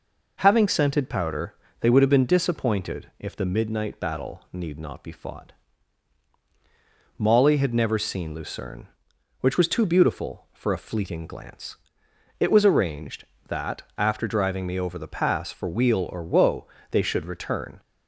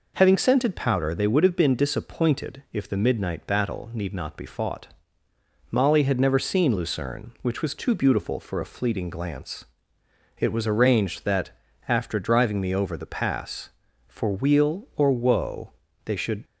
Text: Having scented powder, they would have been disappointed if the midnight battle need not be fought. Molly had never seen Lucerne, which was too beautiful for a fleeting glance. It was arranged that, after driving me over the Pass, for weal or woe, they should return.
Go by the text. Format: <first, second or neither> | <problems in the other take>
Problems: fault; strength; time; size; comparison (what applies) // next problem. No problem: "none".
first | stops before "return"; at 16.4 s